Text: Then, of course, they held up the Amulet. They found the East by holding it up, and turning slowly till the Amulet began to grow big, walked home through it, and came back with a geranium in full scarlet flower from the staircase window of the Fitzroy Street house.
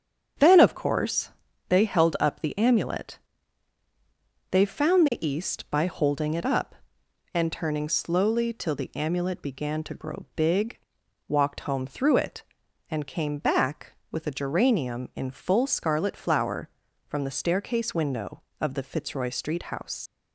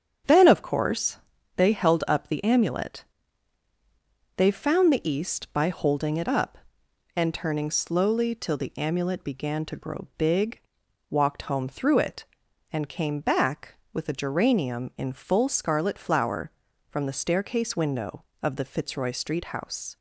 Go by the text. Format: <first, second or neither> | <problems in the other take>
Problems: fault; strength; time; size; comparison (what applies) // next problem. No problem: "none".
second | starts louder than the rest; strong; until 1.7 s; 8 dB; strong in the second // leaves "house" unfinished; at 20.0 s; 90 ms